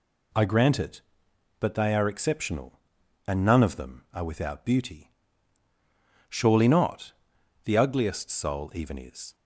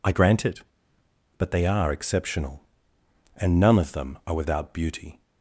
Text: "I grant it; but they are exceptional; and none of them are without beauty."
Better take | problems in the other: second | goes on to say "Surely not The ugliest soul even is"; strong; from 6.2 s on; 3.0 s long

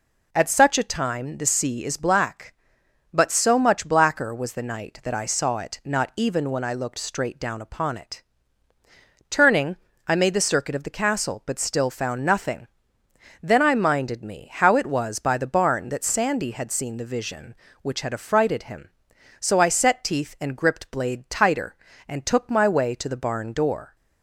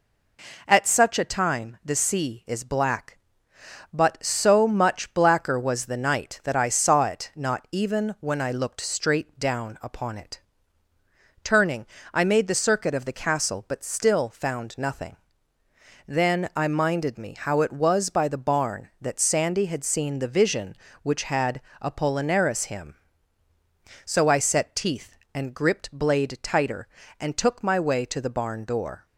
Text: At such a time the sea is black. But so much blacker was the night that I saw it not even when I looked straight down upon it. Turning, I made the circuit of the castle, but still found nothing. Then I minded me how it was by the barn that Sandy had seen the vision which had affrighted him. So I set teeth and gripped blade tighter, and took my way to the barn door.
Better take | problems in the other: first | says "apollinaris" for "affrighted"; at 21.8 s

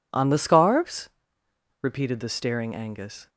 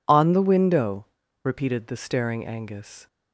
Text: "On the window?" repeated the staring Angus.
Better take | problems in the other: second | says "scarves" for "window"; at 0.3 s

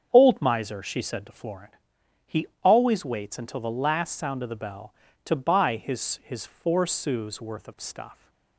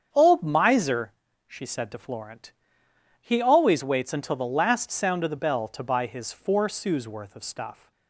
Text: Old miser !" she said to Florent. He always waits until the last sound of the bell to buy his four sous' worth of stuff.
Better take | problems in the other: second | starts louder than the rest; strong; until 1.1 s; 7 dB; strong in the second // pauses between "He" and "always"; slight; at 2.4 s; 0.16 s long // says "his" twice; at 6.2 s

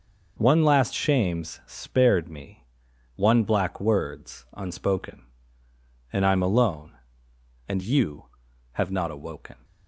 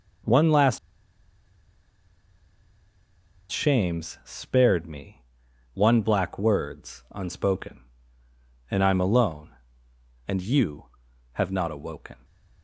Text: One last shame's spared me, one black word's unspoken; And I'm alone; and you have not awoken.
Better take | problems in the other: first | pauses between "last" and "shame's"; strong; at 0.7 s; 2.7 s long

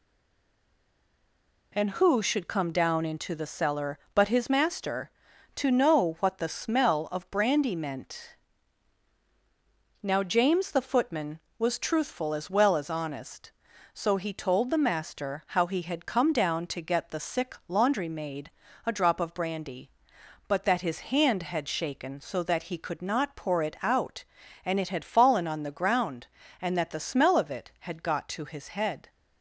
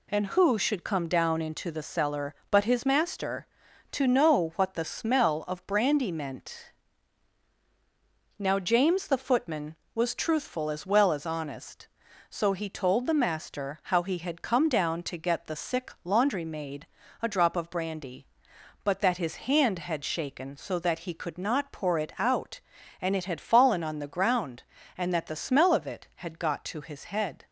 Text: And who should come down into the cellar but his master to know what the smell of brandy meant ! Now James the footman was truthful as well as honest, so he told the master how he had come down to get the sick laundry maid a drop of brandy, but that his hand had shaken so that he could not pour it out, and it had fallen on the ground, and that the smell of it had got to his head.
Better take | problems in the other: second | stays silent before the first word; noticeable; until 1.7 s; 1.7 s long // pauses between "maid" and "a"; slight; at 18.5 s; 0.34 s long; slight in the second

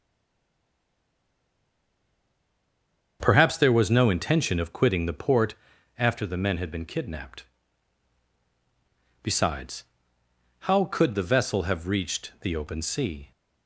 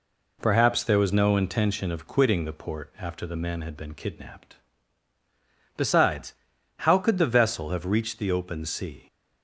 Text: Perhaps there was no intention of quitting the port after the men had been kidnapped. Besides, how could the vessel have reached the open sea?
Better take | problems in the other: second | stays silent before the first word; strong; until 3.1 s; 3.1 s long // starts louder than the rest; strong; until 4.2 s; 7 dB // pauses between "port" and "after"; at 5.5 s; 0.44 s long

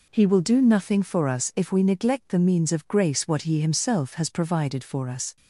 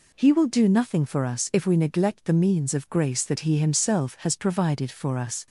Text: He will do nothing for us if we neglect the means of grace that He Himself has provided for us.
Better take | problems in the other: second | says "what" for "that"; at 3.2 s

